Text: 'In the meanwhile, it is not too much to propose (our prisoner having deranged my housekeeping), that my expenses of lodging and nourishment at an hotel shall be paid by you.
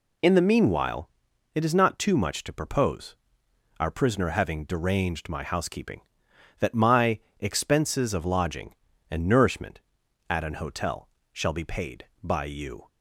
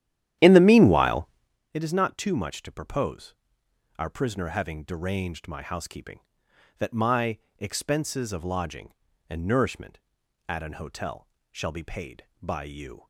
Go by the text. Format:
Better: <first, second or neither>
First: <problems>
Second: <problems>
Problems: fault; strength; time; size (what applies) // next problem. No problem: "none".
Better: first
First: pauses between "my" and "expenses"; slight; at 7.1 s; 0.20 s long // pauses between "hotel" and "shall"; slight; at 11.0 s; 0.24 s long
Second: starts louder than the rest; strong; until 1.6 s; 11.5 dB // pauses between "my" and "expenses"; slight; at 7.3 s; 0.20 s long // pauses between "hotel" and "shall"; slight; at 11.2 s; 0.24 s long